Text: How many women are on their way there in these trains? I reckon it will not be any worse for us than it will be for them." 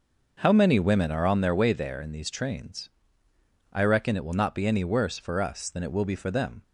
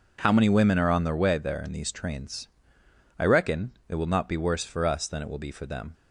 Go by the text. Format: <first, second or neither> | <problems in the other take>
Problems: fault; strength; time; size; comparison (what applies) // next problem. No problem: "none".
first | pauses between "reckon" and "it"; slight; at 3.7 s; 0.16 s long // skips "any"; at 4.3 s